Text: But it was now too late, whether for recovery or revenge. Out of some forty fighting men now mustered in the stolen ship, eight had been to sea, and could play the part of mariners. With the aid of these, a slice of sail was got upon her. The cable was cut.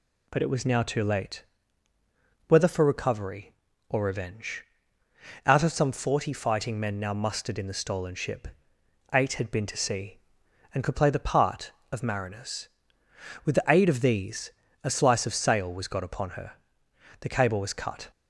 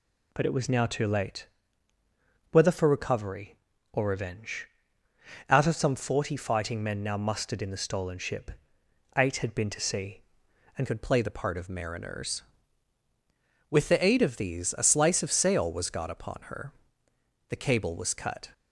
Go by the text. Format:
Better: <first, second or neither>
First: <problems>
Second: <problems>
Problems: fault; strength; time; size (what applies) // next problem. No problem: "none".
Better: first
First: none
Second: changes voice at "could"; from 10.8 s on; 7.6 s long